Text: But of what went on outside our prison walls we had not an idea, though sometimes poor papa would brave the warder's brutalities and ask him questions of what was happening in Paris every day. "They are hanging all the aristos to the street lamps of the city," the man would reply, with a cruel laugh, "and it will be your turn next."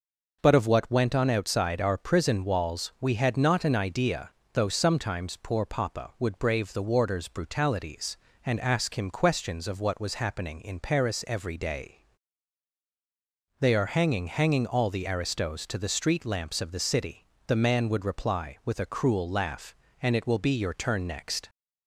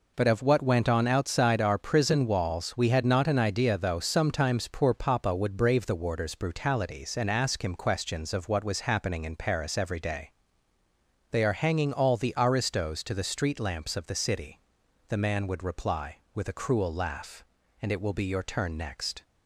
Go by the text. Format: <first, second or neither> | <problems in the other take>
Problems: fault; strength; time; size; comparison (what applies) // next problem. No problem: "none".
second | says "hanging" twice; at 14.2 s